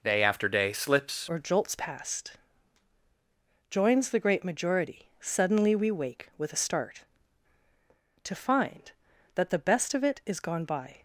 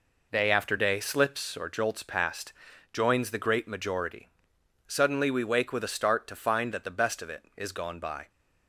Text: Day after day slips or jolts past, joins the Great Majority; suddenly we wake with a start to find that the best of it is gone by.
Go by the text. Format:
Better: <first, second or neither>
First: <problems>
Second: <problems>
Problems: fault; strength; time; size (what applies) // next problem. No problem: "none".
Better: second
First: changes voice at "or"; from 1.2 s on; 9.8 s long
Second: none